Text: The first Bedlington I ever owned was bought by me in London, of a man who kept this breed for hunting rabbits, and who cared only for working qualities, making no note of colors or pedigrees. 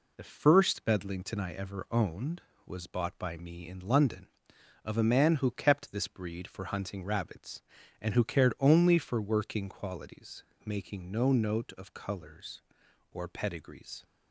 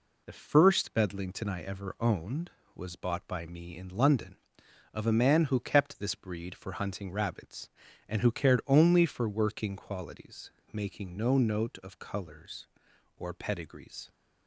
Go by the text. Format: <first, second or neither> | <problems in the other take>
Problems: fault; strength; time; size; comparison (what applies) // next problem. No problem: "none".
neither | none